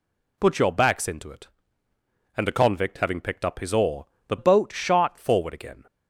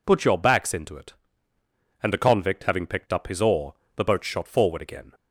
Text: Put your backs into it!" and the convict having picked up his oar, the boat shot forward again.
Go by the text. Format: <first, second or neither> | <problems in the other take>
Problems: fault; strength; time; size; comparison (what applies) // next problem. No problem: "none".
second | changes voice from "boat" to "shot"; from 4.3 to 5.1 s; 0.8 s long